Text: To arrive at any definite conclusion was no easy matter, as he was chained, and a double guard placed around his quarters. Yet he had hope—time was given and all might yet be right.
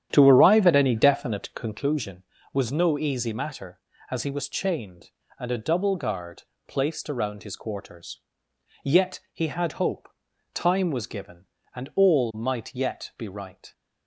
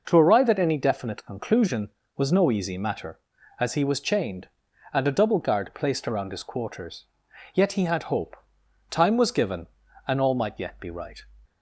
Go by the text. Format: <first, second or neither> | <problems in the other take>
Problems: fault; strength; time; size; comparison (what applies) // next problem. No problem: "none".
second | starts louder than the rest; strong; until 1.9 s; 10 dB // pauses between "guard" and "placed"; slight; at 6.4 s; 0.24 s long